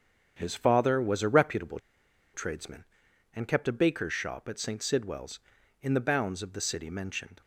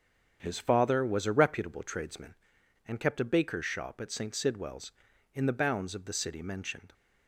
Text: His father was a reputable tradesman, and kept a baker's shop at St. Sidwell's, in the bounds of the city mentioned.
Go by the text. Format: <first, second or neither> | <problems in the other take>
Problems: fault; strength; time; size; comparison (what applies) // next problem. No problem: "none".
second | starts louder than the rest; strong; until 1.3 s; 7.5 dB; strong in the second // pauses between "reputable" and "tradesman"; noticeable; at 1.7 s; 0.54 s long